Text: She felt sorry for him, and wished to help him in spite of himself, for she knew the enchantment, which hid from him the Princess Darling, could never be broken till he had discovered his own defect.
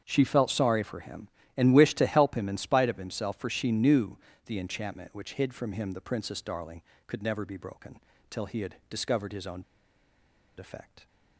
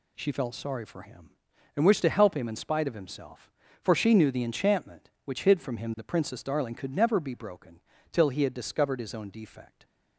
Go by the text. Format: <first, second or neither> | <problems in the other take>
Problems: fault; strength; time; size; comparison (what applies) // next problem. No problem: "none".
second | starts louder than the rest; strong; until 1.0 s; 7.5 dB // pauses between "knew" and "the"; slight; at 4.1 s; 0.30 s long // pauses between "broken" and "till"; slight; at 7.9 s; 0.30 s long; slight in the second // pauses between "own" and "defect"; noticeable; at 9.6 s; 0.96 s long